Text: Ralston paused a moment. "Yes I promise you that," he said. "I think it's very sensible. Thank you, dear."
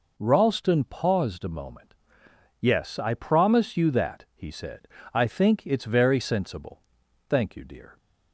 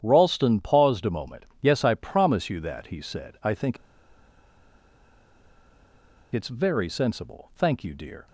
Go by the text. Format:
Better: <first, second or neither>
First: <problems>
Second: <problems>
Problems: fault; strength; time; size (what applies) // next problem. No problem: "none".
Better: first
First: none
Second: starts louder than the rest; strong; until 1.0 s; 9.5 dB // pauses between "think" and "it's"; strong; at 3.7 s; 2.5 s long